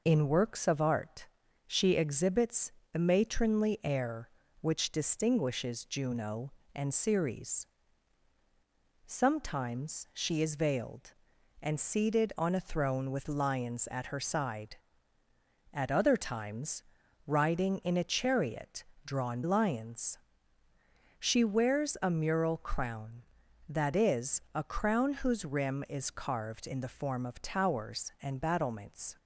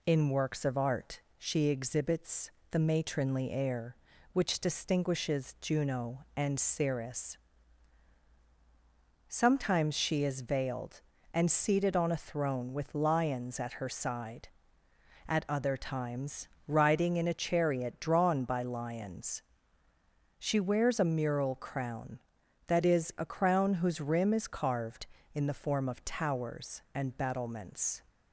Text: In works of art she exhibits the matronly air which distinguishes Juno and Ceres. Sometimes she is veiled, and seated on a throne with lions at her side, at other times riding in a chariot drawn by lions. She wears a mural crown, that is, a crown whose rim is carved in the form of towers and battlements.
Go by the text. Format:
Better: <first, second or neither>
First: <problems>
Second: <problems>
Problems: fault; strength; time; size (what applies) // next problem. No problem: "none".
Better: second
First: pauses between "art" and "she"; at 1.2 s; 0.40 s long // pauses between "exhibits" and "the"; slight; at 2.7 s; 0.22 s long // pauses between "times" and "riding"; noticeable; at 16.8 s; 0.46 s long // pauses between "chariot" and "drawn"; slight; at 18.8 s; 0.20 s long // skips "by"; at 19.4 s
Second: pauses between "art" and "she"; slight; at 1.1 s; 0.18 s long // pauses between "exhibits" and "the"; slight; at 2.4 s; 0.22 s long // pauses between "times" and "riding"; slight; at 16.4 s; 0.20 s long